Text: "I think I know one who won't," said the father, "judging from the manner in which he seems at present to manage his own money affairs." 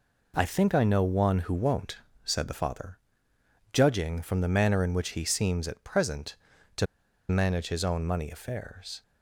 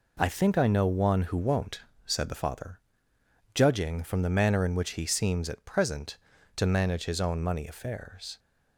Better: second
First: pauses between "to" and "manage"; at 6.8 s; 0.44 s long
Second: none

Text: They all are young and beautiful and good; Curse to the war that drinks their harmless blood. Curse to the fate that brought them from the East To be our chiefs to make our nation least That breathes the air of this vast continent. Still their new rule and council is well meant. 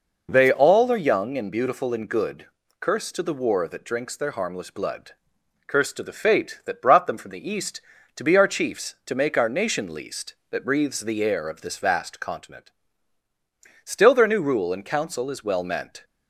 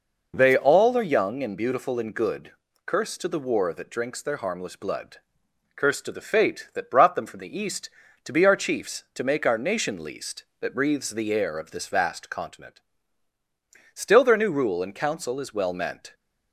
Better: neither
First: none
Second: none

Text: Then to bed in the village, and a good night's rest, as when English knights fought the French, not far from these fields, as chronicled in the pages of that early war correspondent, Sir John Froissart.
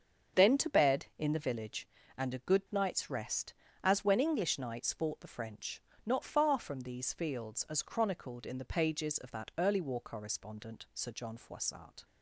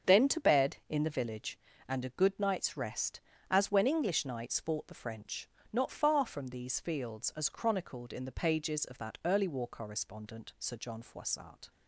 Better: neither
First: starts louder than the rest; strong; until 1.4 s; 7 dB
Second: starts louder than the rest; until 1.1 s; 7 dB

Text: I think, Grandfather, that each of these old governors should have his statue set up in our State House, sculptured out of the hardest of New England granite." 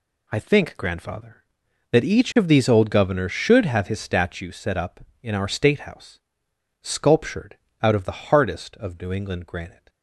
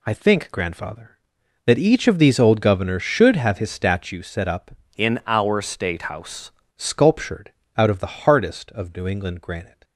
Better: first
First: pauses between "sculptured" and "out"; slight; at 7.5 s; 0.26 s long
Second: changes voice from "in" to "House"; from 4.9 to 6.5 s; 1.6 s long // pauses between "sculptured" and "out"; slight; at 7.5 s; 0.26 s long

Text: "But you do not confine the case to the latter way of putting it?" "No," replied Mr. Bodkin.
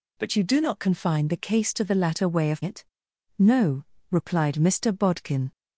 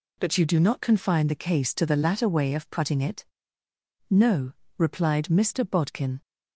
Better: second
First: skips "putting"; at 2.6 s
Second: none

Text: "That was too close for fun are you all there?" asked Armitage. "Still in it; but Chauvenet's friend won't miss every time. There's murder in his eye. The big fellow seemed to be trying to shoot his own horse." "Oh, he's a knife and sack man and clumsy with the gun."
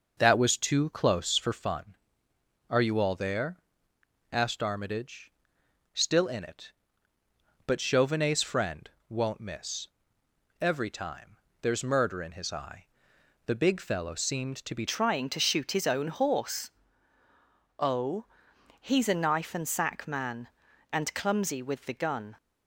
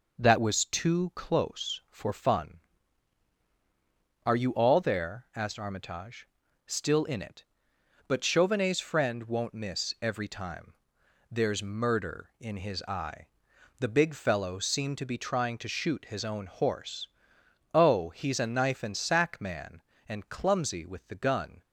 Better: second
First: pauses between "friend" and "won't"; slight; at 8.9 s; 0.18 s long // pauses between "miss" and "every"; noticeable; at 9.8 s; 0.74 s long // changes voice at "trying"; from 14.8 s on; 7.5 s long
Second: none

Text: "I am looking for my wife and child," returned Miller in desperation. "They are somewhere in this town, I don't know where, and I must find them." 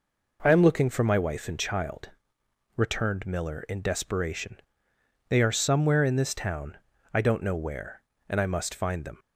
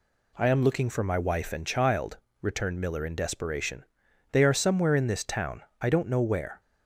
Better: first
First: none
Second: stops before "and I must find them"; at 6.6 s

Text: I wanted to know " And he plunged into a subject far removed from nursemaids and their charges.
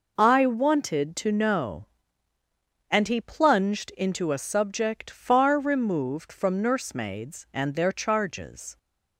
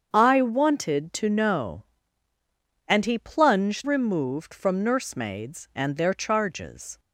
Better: first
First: none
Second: starts louder than the rest; strong; until 1.1 s; 7.5 dB // skips "into a subject far"; at 3.8 s

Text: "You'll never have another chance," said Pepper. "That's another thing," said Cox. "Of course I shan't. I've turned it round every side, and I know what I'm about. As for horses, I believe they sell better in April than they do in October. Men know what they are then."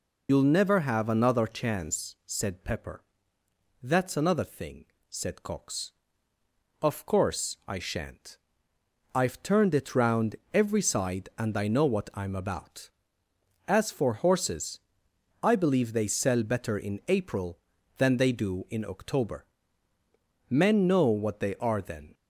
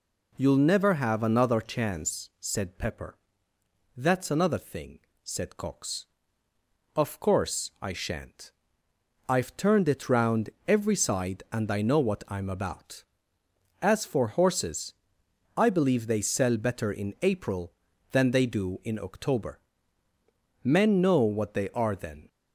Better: second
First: loses the start of "You'll"; at 0.2 s; 90 ms // pauses between "round" and "every"; slight; at 10.3 s; 0.18 s long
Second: pauses between "round" and "every"; slight; at 10.4 s; 0.18 s long

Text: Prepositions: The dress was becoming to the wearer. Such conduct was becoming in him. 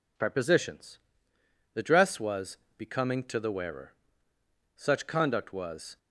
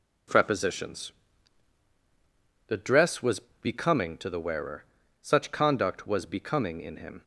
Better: second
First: pauses between "was" and "becoming"; slight; at 2.5 s; 0.22 s long // stops before "becoming in him"; at 5.9 s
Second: pauses between "was" and "becoming"; slight; at 3.3 s; 0.24 s long

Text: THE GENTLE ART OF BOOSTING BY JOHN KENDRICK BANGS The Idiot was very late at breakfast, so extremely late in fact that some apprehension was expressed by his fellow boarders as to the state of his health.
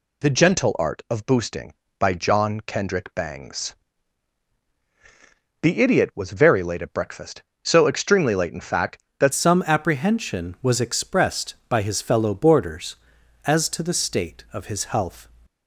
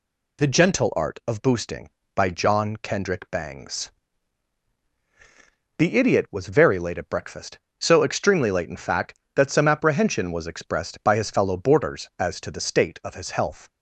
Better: second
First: pauses between "BANGS" and "The"; strong; at 3.7 s; 1.8 s long // changes voice at "some"; from 9.3 s on; 5.9 s long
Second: pauses between "BANGS" and "The"; strong; at 3.9 s; 1.8 s long

